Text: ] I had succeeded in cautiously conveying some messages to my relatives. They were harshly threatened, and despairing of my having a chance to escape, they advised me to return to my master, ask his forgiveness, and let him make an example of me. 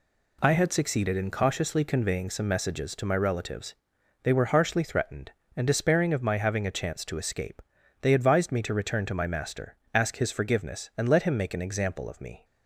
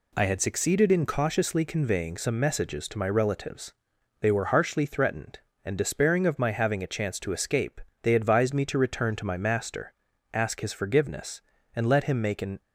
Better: first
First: none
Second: stops before "example of me"; at 12.6 s

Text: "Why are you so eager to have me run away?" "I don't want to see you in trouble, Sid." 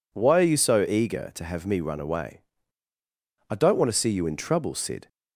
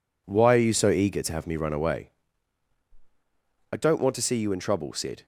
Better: neither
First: none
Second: none

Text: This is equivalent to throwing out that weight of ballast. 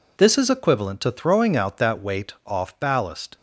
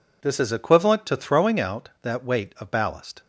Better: second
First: says "off" for "of"; at 2.4 s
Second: none

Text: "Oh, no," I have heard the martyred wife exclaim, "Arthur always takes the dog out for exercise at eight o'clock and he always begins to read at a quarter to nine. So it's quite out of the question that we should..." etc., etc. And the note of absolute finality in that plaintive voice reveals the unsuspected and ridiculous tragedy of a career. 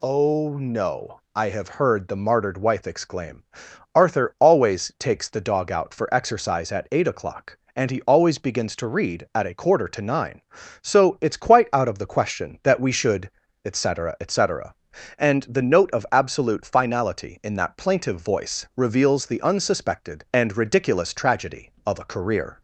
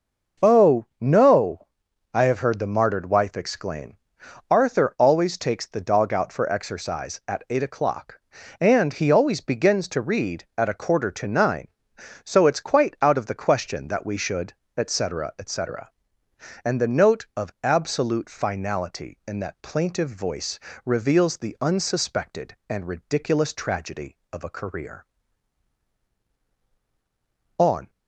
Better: first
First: none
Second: pauses between "voice" and "reveals"; slight; at 20.5 s; 0.26 s long // goes on to say "On"; slight; from 27.5 s on; 0.32 s long

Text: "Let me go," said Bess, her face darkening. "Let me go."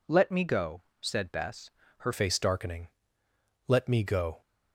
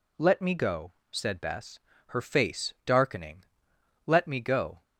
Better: second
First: changes voice at "face"; from 2.1 s on; 2.3 s long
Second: none

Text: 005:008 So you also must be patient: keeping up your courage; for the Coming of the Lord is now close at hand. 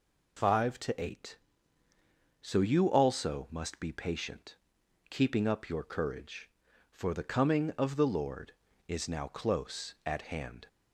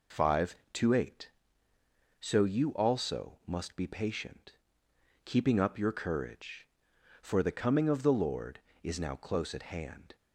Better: neither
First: none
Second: none

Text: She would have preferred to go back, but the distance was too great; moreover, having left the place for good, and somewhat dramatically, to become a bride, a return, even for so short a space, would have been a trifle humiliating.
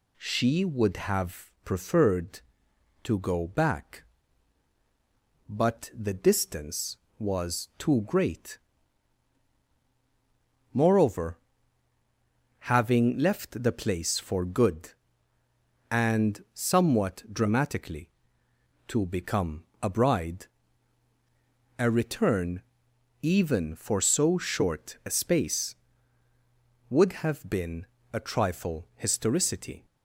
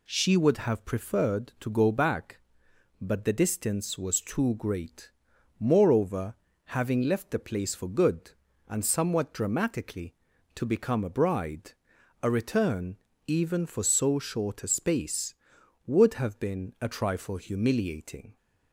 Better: second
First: pauses between "become" and "a"; slight; at 19.6 s; 0.18 s long // pauses between "been" and "a"; slight; at 27.8 s; 0.28 s long // says "historicity" for "humiliating"; at 28.9 s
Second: none

